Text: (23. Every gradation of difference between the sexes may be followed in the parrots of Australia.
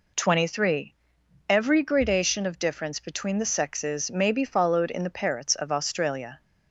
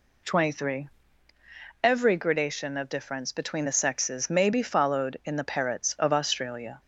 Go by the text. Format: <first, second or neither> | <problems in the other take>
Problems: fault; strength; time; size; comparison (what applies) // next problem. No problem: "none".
neither | none